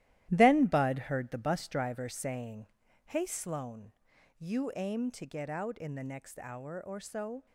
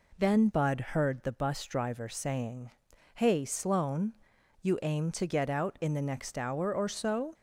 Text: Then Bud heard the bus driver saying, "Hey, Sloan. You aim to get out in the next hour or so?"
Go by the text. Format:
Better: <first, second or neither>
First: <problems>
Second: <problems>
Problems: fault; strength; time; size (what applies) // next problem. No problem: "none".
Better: second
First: gets quieter; strong; throughout; 9 dB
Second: none